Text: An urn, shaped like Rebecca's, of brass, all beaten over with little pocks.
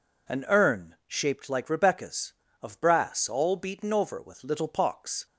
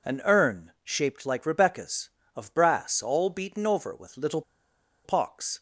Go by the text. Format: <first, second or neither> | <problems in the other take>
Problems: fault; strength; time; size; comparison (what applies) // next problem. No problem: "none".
first | pauses between "little" and "pocks"; noticeable; at 4.4 s; 0.63 s long